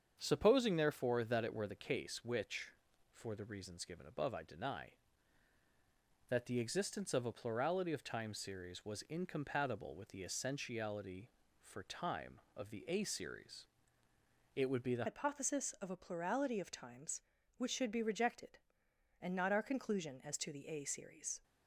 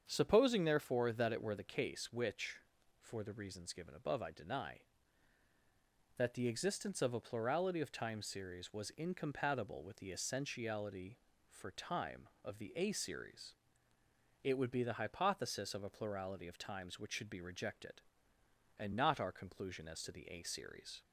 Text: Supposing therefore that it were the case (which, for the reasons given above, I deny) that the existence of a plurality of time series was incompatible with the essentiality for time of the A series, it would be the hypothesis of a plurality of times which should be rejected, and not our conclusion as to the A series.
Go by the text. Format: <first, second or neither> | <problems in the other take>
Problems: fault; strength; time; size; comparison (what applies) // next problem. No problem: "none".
second | starts louder than the rest; strong; until 1.2 s; 7.5 dB; strong in the second // changes voice at "hypothesis"; from 15.0 s on; 6.4 s long